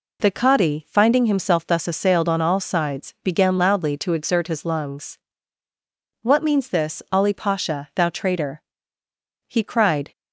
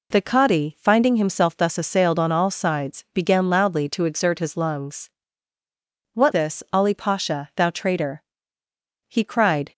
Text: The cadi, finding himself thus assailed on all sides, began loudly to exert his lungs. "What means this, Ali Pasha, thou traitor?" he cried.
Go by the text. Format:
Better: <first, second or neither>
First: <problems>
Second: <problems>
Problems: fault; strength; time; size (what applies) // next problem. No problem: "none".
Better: first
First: none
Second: skips "means"; at 6.3 s